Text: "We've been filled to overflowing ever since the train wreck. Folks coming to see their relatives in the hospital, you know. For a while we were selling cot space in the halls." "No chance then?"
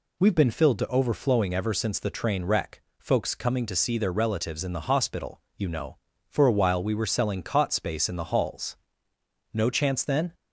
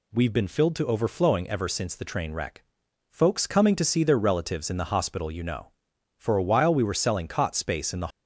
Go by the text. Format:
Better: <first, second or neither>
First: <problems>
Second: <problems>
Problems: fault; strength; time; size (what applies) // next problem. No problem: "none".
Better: first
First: none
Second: stops before "halls No chance then"; at 8.1 s